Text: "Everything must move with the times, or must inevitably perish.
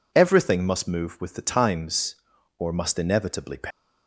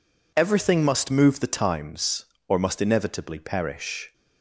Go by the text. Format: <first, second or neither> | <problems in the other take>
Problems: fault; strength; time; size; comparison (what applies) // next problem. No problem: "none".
first | skips "with"; at 1.4 s